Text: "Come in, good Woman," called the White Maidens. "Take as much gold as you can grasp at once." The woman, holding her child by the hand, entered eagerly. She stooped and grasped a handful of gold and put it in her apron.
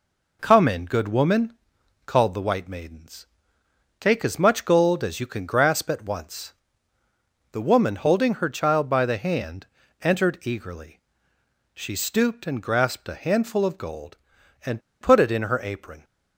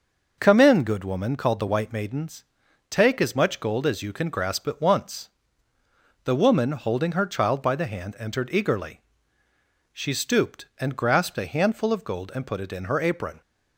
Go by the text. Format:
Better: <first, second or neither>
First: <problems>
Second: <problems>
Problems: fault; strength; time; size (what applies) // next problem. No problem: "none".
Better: second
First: pauses between "and" and "put"; slight; at 14.8 s; 0.21 s long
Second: none